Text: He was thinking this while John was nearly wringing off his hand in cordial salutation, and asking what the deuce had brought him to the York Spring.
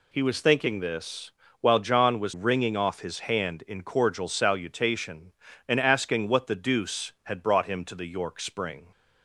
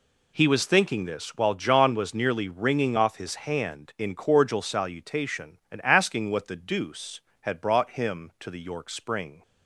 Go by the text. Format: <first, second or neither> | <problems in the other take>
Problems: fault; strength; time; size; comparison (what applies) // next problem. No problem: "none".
second | pauses between "this" and "while"; slight; at 1.3 s; 0.30 s long // skips "nearly"; at 2.3 s